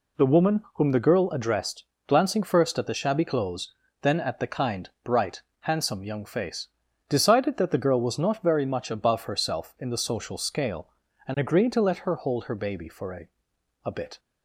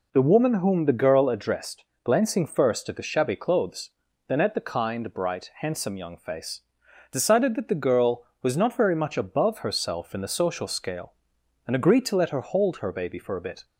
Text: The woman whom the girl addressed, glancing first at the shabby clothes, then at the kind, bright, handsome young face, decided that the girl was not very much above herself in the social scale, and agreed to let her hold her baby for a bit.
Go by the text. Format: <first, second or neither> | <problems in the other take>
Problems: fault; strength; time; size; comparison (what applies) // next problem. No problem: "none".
second | says "a" twice; at 13.8 s